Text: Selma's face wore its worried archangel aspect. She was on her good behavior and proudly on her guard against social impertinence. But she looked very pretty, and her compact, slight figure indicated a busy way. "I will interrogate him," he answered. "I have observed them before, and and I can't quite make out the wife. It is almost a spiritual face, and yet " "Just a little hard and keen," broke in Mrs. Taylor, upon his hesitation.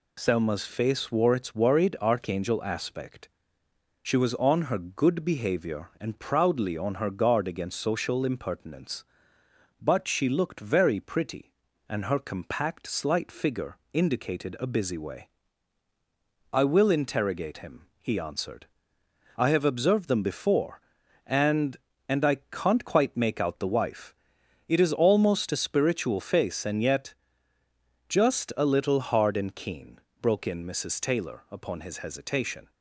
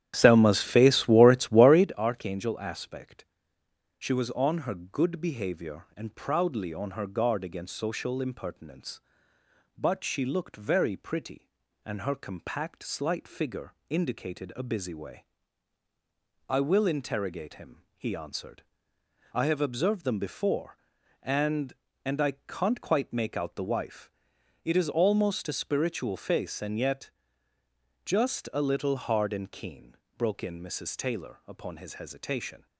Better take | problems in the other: first | starts louder than the rest; strong; until 2.0 s; 11 dB // pauses between "figure" and "indicated"; slight; at 13.7 s; 0.16 s long; slight in the first

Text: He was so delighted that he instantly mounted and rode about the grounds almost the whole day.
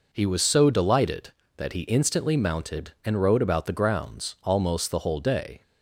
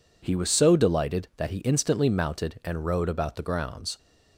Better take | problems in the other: first | stops before "almost the whole day"; at 3.9 s

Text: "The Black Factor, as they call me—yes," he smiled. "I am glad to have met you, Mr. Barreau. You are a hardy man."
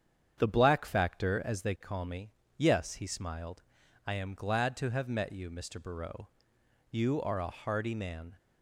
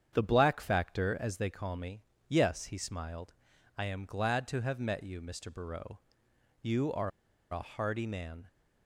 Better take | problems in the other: first | starts louder than the rest; strong; until 1.1 s; 8.5 dB; strong in the first // pauses between "are" and "a"; at 7.0 s; 0.41 s long

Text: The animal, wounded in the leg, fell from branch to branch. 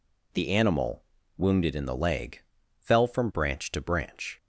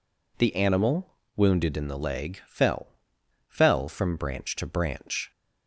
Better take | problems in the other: first | says "fell" twice; at 3.4 s

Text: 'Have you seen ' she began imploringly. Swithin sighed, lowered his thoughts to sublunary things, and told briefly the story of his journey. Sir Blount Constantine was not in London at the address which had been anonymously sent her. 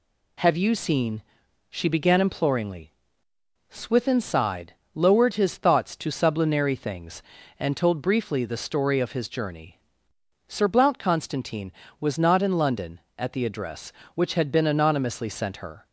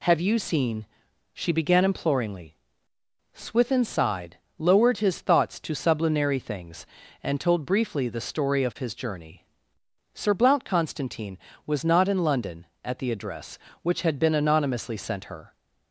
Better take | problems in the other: neither | none

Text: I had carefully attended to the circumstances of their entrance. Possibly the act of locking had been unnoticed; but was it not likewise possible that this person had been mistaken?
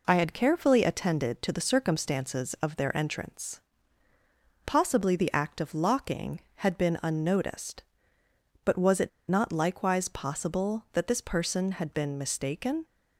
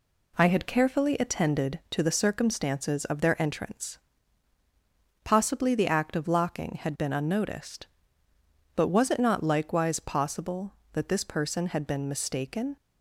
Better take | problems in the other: second | pauses between "it" and "not"; slight; at 9.0 s; 0.21 s long

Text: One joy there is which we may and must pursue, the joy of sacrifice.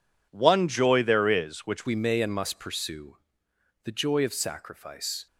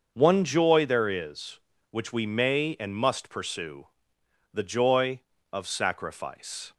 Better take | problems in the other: second | changes voice at "we"; from 1.8 s on; 3.4 s long

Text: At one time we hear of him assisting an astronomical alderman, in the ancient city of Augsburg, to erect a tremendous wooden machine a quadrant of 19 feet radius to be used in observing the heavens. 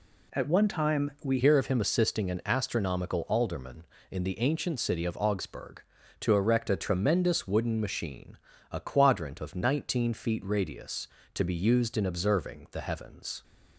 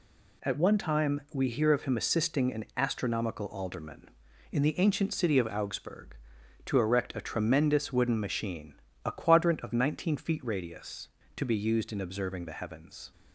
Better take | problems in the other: second | changes voice at "hear"; from 1.3 s on; 12.1 s long // pauses between "machine" and "a"; slight; at 8.3 s; 0.34 s long; slight in the second

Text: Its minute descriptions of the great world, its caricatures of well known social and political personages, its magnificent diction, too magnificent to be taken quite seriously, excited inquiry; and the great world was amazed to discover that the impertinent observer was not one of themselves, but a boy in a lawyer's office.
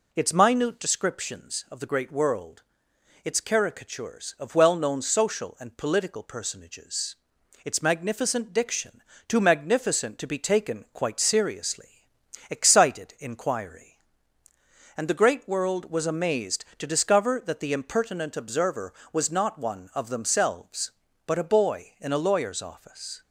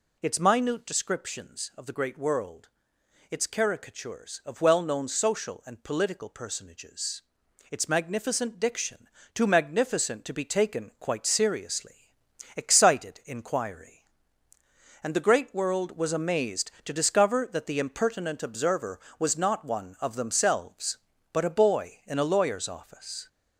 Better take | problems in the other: first | gets louder; noticeable; throughout; 4.5 dB

